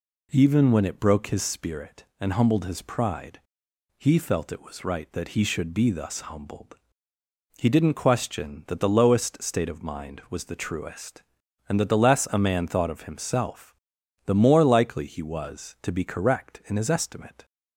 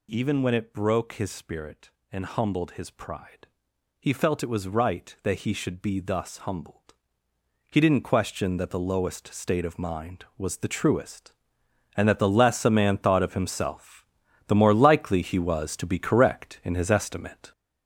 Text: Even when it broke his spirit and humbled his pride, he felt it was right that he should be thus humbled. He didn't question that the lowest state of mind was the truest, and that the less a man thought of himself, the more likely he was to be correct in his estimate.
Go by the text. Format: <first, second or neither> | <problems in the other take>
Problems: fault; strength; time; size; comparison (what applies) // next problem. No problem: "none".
first | gets louder; throughout; 6.5 dB